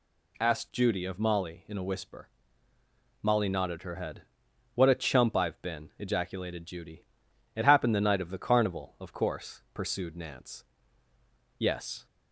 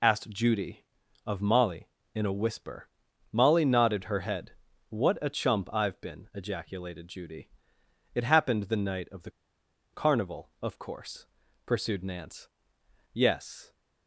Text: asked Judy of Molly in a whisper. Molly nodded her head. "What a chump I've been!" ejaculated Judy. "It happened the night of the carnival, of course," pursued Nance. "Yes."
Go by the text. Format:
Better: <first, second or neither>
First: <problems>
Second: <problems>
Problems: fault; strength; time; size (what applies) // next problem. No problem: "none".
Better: first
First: none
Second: pauses between "the" and "carnival"; noticeable; at 9.3 s; 0.62 s long